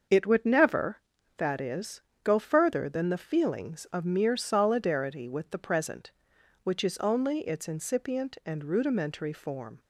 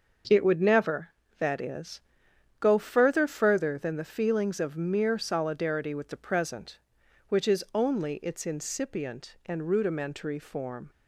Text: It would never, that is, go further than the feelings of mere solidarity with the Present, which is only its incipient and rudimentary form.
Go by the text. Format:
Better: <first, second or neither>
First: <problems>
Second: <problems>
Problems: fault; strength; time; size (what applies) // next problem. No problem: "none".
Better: first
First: starts louder than the rest; until 1.4 s; 6.5 dB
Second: starts louder than the rest; until 1.5 s; 6 dB // says "further" twice; at 3.2 s